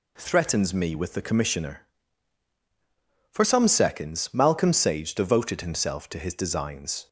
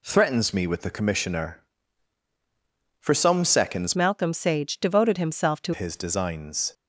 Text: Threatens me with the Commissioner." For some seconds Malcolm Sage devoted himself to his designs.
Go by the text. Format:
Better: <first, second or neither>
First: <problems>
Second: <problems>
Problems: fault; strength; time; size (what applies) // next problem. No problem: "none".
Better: first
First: none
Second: changes voice from "Malcolm" to "to"; from 3.9 to 5.7 s; 1.8 s long